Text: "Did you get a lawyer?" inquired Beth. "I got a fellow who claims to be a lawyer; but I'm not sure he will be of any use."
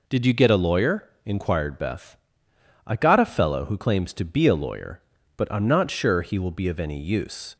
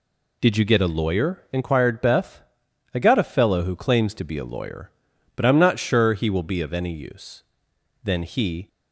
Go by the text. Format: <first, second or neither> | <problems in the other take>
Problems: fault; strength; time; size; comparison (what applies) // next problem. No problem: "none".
first | goes on to say "Then he"; noticeable; from 8.0 s on; 0.64 s long